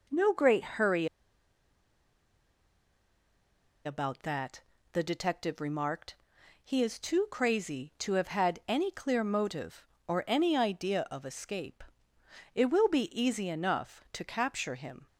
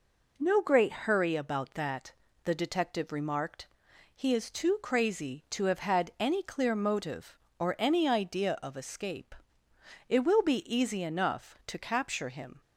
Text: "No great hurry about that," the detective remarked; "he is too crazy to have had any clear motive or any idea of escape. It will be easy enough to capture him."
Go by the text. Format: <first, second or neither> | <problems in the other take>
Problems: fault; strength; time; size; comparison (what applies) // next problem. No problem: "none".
second | pauses between "hurry" and "about"; strong; at 1.0 s; 2.8 s long